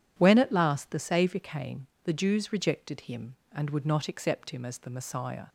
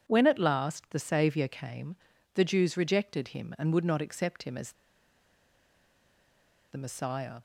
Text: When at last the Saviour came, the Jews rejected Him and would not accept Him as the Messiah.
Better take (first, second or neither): first